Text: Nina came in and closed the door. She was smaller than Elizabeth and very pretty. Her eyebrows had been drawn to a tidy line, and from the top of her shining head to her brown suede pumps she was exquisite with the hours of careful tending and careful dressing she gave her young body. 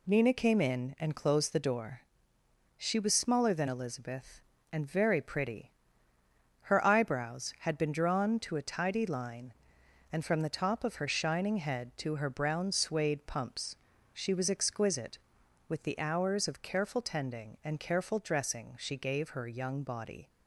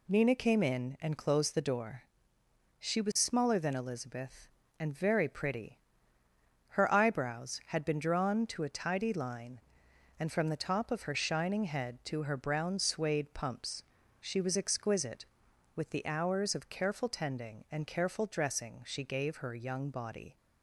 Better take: neither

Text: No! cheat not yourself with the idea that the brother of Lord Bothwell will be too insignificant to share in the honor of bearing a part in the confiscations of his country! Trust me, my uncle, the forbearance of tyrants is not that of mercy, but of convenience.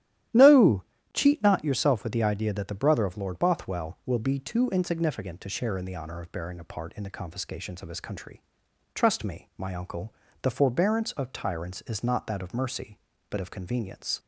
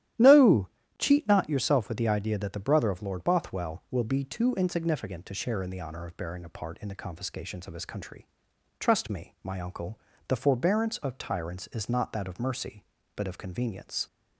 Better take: neither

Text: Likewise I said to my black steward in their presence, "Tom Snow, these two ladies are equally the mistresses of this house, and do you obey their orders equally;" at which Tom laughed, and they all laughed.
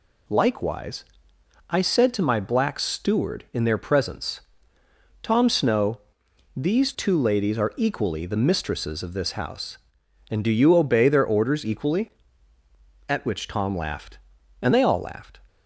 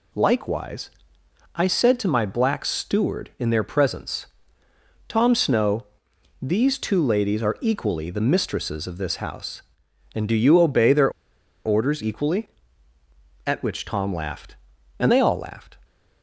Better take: first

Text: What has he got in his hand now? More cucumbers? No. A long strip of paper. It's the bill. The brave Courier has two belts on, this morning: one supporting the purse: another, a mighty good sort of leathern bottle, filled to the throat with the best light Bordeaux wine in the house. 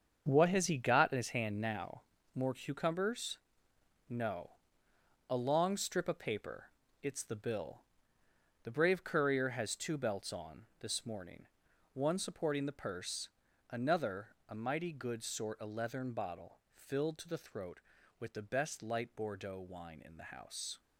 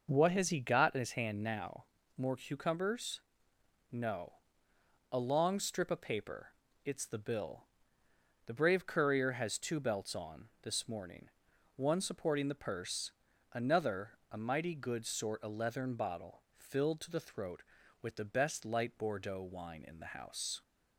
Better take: second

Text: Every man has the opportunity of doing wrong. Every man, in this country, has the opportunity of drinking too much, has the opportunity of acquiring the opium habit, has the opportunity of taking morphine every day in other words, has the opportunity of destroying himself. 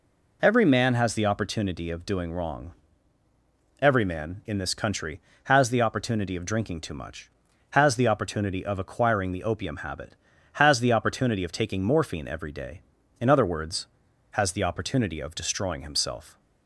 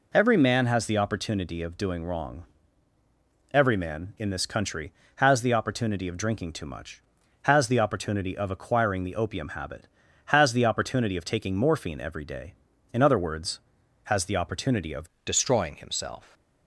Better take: first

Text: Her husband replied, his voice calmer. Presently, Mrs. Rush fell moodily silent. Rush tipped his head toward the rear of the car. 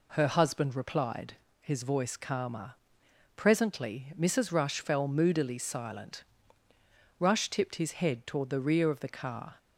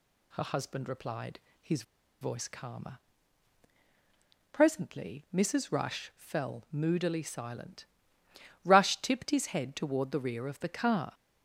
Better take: first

